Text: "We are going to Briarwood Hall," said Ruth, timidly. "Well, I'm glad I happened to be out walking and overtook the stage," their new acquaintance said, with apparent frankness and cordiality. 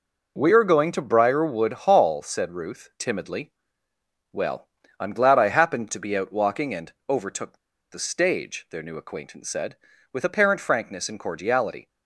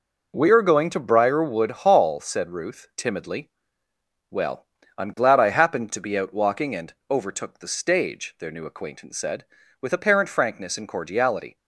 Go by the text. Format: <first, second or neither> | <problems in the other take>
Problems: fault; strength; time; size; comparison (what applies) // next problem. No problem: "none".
second | pauses between "and" and "overtook"; slight; at 6.9 s; 0.16 s long; slight in the second // pauses between "overtook" and "the"; slight; at 7.5 s; 0.34 s long